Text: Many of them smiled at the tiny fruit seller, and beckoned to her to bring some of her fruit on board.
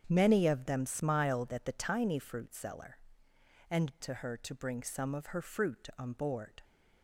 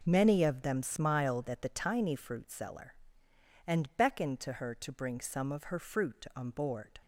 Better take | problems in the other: second | starts louder than the rest; strong; until 1.0 s; 8 dB // skips "beckoned"; at 4.0 s

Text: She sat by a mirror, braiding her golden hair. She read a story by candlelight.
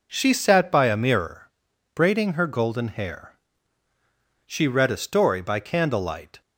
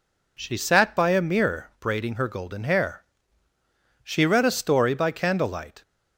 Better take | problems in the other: neither | none

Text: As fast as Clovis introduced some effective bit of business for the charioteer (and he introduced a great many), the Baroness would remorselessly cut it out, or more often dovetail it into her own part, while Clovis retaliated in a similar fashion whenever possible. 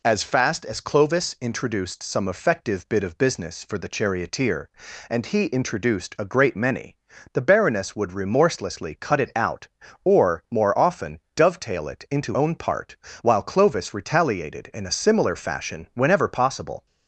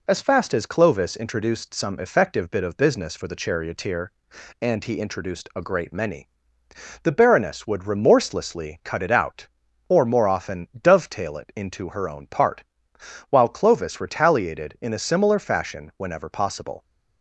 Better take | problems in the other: second | pauses between "often" and "dovetail"; slight; at 11.1 s; 0.16 s long // skips "her"; at 12.3 s

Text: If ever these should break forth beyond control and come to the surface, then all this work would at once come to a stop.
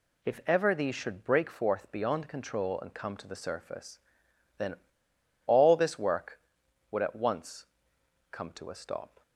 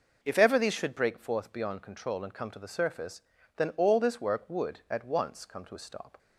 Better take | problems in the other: second | pauses between "then" and "all"; noticeable; at 4.7 s; 0.70 s long // pauses between "once" and "come"; noticeable; at 7.6 s; 0.64 s long

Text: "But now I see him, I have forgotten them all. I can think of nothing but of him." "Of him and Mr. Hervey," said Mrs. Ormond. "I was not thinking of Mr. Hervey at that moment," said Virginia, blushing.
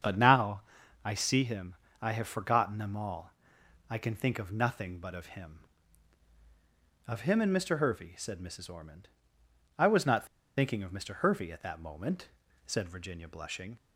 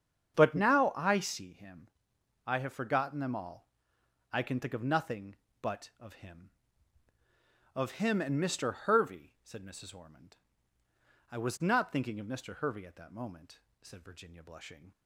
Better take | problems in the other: second | starts louder than the rest; strong; until 1.4 s; 7.5 dB; strong in the second // pauses between "now" and "I"; at 0.6 s; 0.42 s long // pauses between "not" and "thinking"; slight; at 10.2 s; 0.32 s long

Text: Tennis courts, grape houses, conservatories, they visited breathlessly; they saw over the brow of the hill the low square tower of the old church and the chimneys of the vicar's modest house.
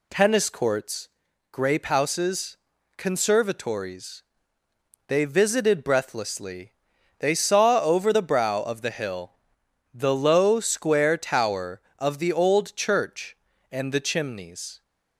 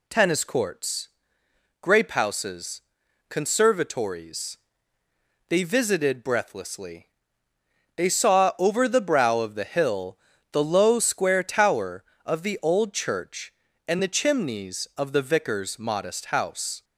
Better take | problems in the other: second | pauses between "hill" and "the"; noticeable; at 9.3 s; 0.56 s long; slight in the second // stops before "of the vicar's modest house"; at 14.8 s

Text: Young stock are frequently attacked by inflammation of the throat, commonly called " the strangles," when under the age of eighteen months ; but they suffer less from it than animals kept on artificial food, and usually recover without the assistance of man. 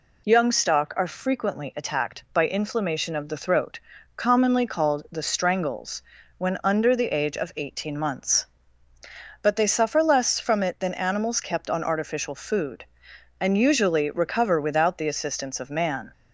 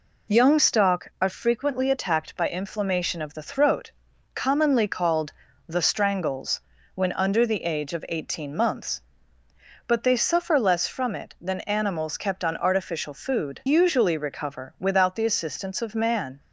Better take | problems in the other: first | skips "and"; at 13.6 s

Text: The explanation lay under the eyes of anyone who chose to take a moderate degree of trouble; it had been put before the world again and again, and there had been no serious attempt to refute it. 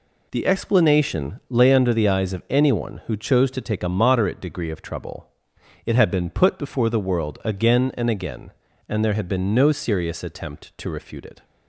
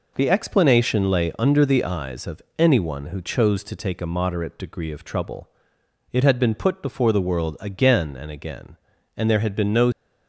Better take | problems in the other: first | pauses between "of" and "anyone"; slight; at 2.4 s; 0.18 s long // stops before "serious attempt to refute it"; at 9.9 s

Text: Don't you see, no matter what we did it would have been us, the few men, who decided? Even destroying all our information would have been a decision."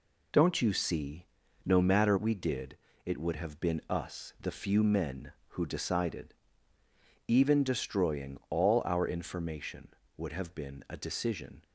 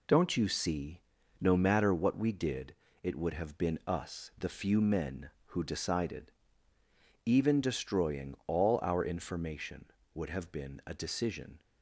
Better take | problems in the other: second | skips "what"; at 2.1 s // pauses between "did" and "it"; slight; at 2.7 s; 0.28 s long; slight in the second

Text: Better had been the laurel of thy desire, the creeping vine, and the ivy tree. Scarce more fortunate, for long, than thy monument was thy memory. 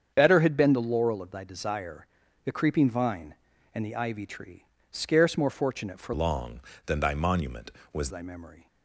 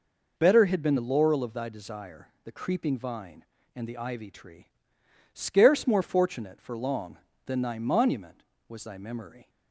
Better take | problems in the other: second | starts louder than the rest; strong; until 1.1 s; 7.5 dB // changes voice from "long" to "was"; from 6.1 to 8.0 s; 1.9 s long

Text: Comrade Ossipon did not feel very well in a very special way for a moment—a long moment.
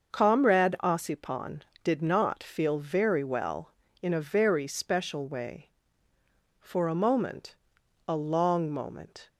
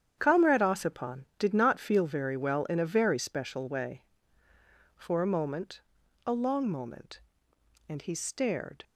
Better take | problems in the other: first | starts louder than the rest; strong; until 1.1 s; 9 dB; also in the first // goes on to say "And he stared"; noticeable; from 7.8 s on; 0.96 s long

